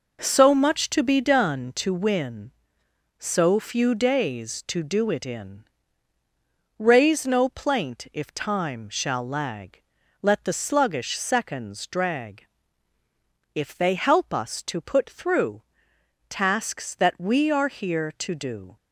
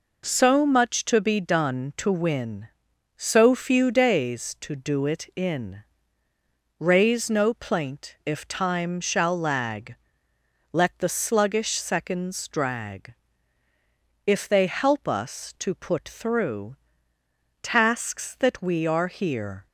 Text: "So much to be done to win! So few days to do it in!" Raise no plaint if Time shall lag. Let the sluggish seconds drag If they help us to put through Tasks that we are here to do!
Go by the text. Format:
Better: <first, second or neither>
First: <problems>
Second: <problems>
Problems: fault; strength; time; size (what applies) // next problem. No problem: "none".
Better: first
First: pauses between "drag" and "If"; at 12.4 s; 1.0 s long // pauses between "through" and "Tasks"; noticeable; at 15.6 s; 0.66 s long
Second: pauses between "drag" and "If"; at 13.1 s; 1.1 s long // pauses between "through" and "Tasks"; noticeable; at 16.7 s; 0.84 s long // stops before "to do"; at 19.6 s